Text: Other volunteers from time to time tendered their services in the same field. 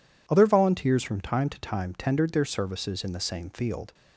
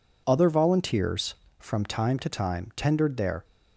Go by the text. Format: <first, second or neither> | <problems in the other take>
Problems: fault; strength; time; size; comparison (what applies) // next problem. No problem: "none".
first | stops before "services in the same field"; at 3.4 s